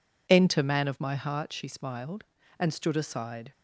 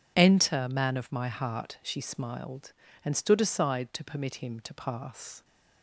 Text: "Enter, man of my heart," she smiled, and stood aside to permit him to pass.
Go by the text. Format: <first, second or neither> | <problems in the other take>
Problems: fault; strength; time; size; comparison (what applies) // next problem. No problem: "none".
second | stops before "to permit him to pass"; at 3.5 s